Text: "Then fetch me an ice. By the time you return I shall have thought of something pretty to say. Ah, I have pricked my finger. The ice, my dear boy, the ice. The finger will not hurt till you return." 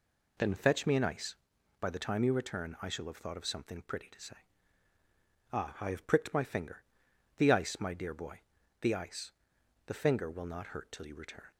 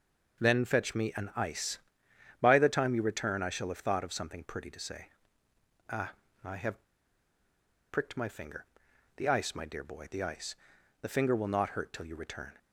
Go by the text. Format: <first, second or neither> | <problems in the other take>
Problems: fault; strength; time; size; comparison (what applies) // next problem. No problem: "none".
first | pauses between "have" and "pricked"; at 6.8 s; 1.0 s long